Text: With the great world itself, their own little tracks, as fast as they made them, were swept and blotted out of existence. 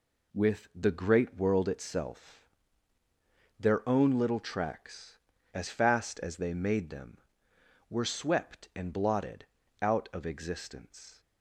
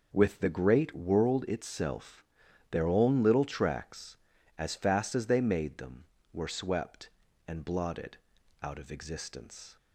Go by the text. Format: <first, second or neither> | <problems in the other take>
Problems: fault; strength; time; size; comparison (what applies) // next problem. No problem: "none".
neither | pauses between "blotted" and "out"; the same in both